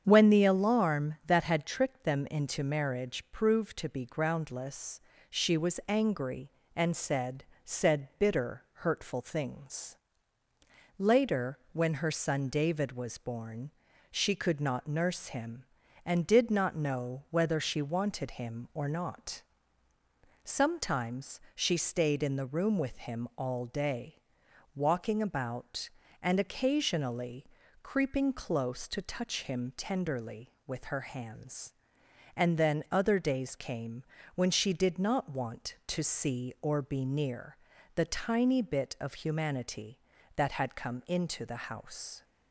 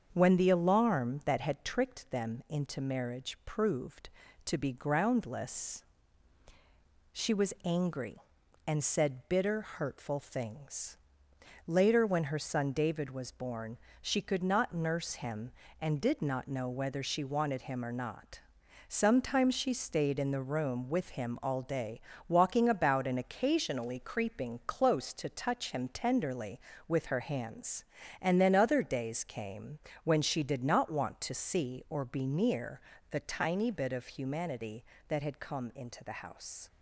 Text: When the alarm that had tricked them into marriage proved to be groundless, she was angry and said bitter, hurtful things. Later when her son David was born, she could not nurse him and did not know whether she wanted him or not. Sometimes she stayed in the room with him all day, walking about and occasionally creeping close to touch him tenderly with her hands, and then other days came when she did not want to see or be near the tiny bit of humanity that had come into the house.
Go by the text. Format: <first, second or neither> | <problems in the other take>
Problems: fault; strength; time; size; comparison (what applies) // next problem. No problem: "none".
second | starts louder than the rest; strong; until 1.0 s; 7.5 dB; also in the second // says "said" twice; at 7.6 s // pauses between "Sometimes" and "she"; slight; at 21.3 s; 0.16 s long // pauses between "occasionally" and "creeping"; slight; at 27.4 s; 0.34 s long // pauses between "came" and "when"; slight; at 34.0 s; 0.32 s long; slight in the second // pauses between "near" and "the"; slight; at 37.5 s; 0.36 s long; slight in the second